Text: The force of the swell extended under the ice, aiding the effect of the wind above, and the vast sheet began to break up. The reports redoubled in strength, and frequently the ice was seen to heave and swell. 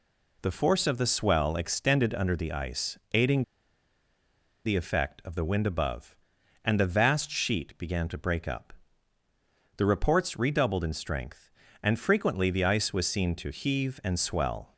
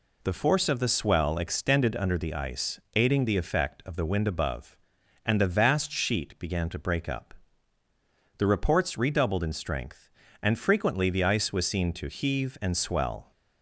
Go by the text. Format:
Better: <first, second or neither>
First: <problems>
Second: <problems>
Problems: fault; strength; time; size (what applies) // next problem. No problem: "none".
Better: second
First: pauses between "aiding" and "the"; at 3.4 s; 1.2 s long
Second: none